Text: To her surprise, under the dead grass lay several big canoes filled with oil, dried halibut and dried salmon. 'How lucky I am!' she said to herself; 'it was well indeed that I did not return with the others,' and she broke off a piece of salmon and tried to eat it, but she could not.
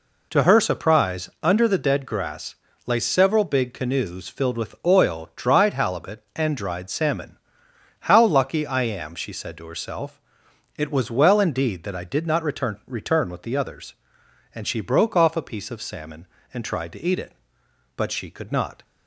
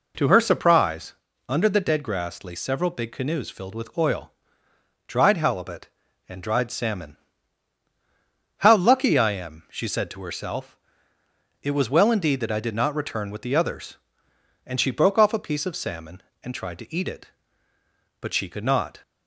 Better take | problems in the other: second | pauses between "grass" and "lay"; slight; at 2.5 s; 0.30 s long // says "return" twice; at 12.8 s

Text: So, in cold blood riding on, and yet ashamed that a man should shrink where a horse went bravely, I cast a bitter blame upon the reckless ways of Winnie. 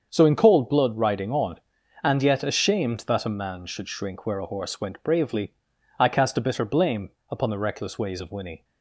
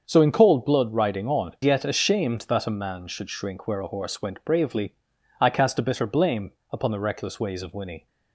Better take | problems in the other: first | starts louder than the rest; until 1.0 s; 7 dB; also in the first // skips "and"; at 1.5 s // pauses between "blame" and "upon"; slight; at 6.5 s; 0.20 s long; slight in the first

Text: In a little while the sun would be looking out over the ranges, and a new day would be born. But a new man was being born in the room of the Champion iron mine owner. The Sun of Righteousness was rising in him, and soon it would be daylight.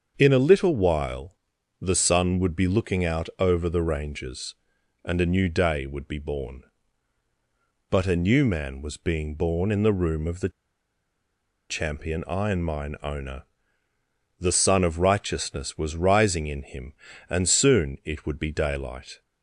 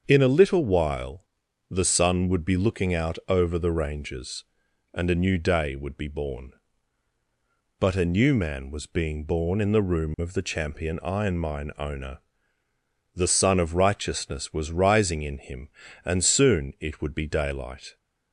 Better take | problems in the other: second | starts louder than the rest; until 1.2 s; 7 dB; also in the second // pauses between "while" and "the"; noticeable; at 1.3 s; 0.46 s long; noticeable in the second // pauses between "the" and "Champion"; at 10.4 s; 1.2 s long

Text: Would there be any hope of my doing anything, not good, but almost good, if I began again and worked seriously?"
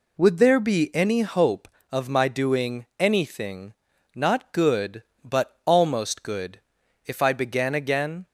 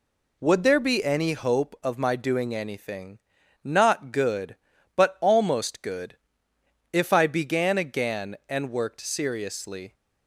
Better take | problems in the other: second | stops before "and worked seriously"; at 8.2 s

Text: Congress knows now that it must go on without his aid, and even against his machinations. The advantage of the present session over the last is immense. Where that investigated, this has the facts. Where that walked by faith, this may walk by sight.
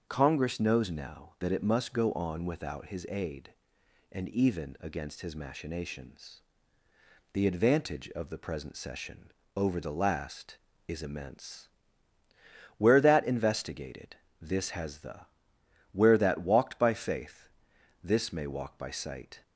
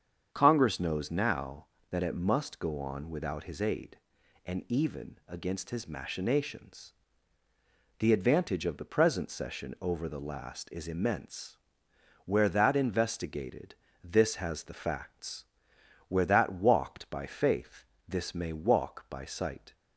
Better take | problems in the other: second | starts louder than the rest; until 1.0 s; 6.5 dB; strong in the second // pauses between "session" and "over"; slight; at 9.3 s; 0.22 s long // skips "facts"; at 15.5 s

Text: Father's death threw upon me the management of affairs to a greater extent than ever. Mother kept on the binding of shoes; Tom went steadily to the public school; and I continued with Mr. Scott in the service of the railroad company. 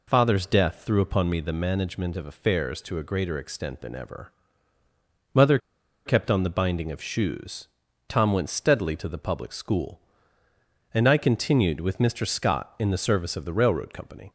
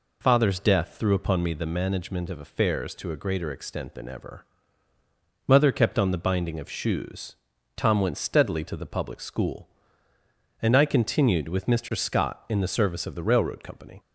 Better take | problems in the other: second | pauses between "Mother" and "kept"; noticeable; at 5.5 s; 0.47 s long

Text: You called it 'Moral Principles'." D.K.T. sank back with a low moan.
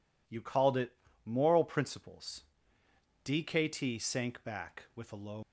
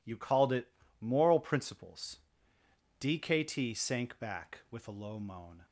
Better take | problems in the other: second | pauses between "it" and "Moral"; slight; at 0.9 s; 0.28 s long; slight in the second // stops before "moan"; at 5.4 s

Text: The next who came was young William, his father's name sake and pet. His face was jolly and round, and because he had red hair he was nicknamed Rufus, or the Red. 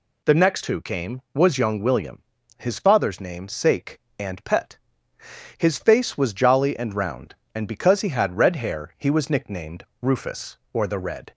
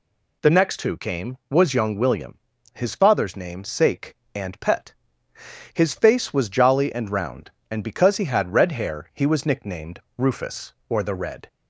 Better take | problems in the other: neither | pauses between "nicknamed" and "Rufus"; slight; the same in both

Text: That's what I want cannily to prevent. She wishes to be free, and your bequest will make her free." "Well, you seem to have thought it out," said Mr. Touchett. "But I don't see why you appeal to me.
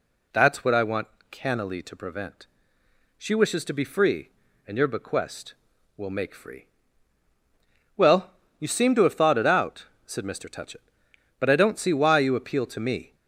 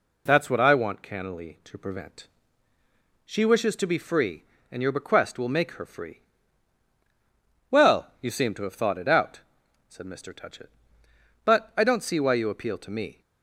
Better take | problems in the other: second | pauses between "want" and "cannily"; slight; at 1.0 s; 0.22 s long // skips "her"; at 6.3 s

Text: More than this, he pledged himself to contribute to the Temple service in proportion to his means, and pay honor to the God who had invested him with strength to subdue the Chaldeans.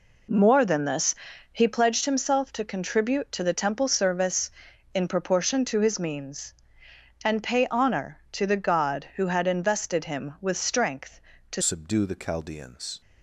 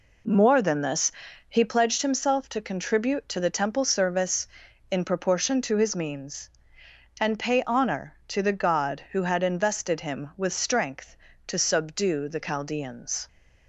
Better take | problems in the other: second | changes voice at "subdue"; from 11.6 s on; 1.4 s long

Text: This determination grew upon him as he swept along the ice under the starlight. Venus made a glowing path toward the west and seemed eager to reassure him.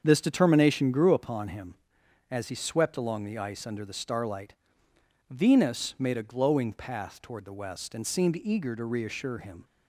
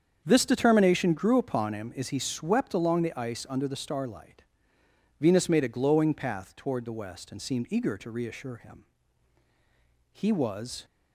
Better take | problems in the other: first | starts louder than the rest; strong; until 1.2 s; 7.5 dB; strong in the first // goes on to say "He was"; noticeable; from 10.1 s on; 0.72 s long

